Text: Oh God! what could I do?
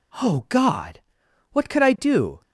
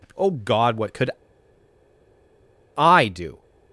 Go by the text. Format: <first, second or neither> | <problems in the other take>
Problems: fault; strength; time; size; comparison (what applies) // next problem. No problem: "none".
first | pauses between "could" and "I"; strong; at 1.1 s; 1.6 s long